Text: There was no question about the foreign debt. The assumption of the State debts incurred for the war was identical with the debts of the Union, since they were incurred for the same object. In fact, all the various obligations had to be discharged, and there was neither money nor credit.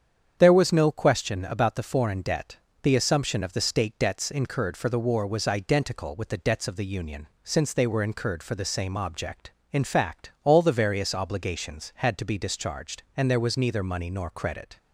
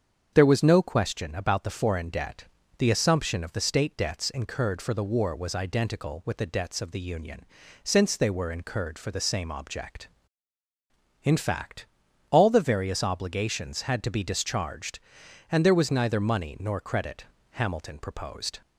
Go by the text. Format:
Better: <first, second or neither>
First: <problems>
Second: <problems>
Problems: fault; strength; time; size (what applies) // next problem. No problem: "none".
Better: first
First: starts louder than the rest; strong; until 1.4 s; 8 dB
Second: starts louder than the rest; strong; until 1.3 s; 7.5 dB // goes on to say "Hamilton proposed"; noticeable; from 17.5 s on; 1.1 s long